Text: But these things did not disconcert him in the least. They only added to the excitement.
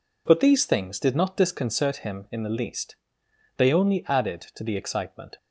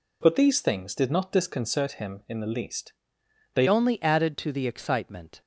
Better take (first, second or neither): first